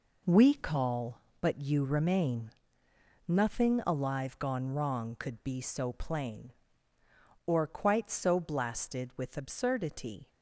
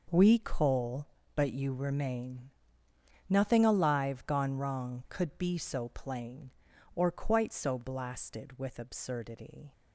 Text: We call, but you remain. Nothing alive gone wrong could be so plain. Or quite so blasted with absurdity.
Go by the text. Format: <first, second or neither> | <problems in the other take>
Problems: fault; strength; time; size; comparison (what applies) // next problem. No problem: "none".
first | says "coal" for "call"; at 0.3 s